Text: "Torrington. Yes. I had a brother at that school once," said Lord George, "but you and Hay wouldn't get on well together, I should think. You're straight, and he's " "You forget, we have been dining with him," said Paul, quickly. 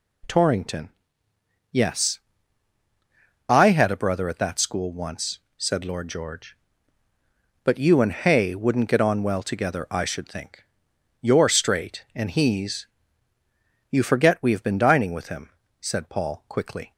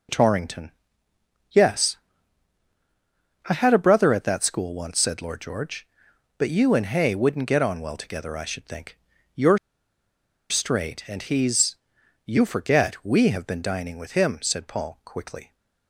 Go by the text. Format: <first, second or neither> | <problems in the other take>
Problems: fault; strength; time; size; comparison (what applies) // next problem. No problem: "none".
first | pauses between "You're" and "straight"; noticeable; at 9.5 s; 0.92 s long